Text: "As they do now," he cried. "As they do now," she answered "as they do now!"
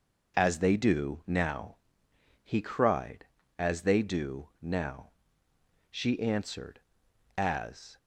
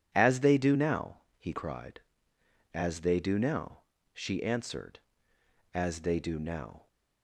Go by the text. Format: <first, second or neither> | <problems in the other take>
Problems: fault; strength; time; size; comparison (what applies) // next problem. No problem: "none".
second | stops before "they do now"; at 7.9 s